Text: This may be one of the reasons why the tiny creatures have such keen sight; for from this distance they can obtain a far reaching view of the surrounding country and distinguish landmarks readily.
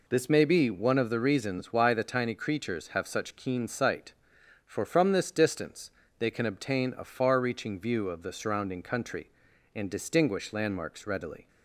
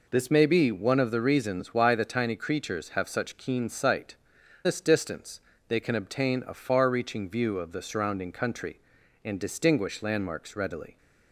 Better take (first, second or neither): first